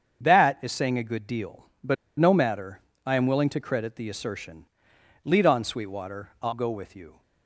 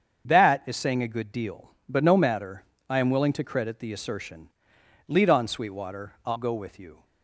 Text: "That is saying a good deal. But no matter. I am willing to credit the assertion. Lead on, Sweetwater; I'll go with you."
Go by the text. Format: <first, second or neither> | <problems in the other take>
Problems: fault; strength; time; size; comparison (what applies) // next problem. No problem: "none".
second | starts louder than the rest; strong; until 1.2 s; 7.5 dB; strong in the second // pauses between "But" and "no"; slight; at 1.9 s; 0.23 s long